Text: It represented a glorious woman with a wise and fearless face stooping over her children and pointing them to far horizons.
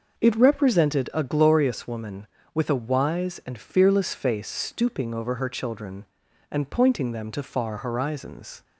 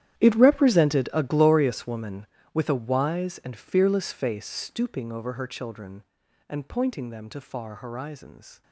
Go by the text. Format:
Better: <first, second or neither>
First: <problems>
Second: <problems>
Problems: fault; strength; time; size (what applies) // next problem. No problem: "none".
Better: first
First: none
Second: gets quieter; strong; throughout; 16.5 dB